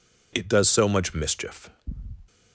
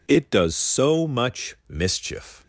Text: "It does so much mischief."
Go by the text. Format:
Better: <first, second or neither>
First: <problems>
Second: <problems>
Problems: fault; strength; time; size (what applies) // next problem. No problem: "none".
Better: neither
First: none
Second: none